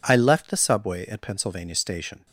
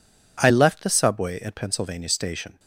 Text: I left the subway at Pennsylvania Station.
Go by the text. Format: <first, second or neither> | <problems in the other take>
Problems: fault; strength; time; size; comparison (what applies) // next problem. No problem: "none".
neither | none